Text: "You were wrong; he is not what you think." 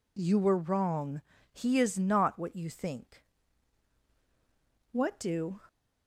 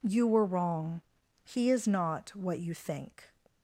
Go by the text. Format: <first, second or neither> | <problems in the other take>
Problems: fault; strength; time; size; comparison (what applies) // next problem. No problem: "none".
second | goes on to say "What do"; noticeable; from 4.9 s on; 0.68 s long